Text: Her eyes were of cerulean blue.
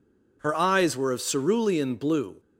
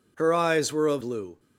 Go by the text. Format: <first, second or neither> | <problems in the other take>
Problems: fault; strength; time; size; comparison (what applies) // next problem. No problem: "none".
first | skips "cerulean"; at 1.0 s